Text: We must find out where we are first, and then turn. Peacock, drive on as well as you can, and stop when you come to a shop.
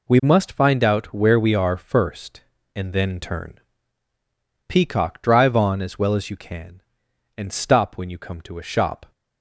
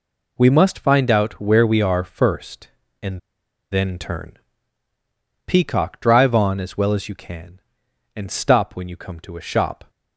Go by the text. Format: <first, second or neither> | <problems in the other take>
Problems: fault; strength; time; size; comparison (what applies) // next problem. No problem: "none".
first | pauses between "and" and "then"; noticeable; at 3.1 s; 0.52 s long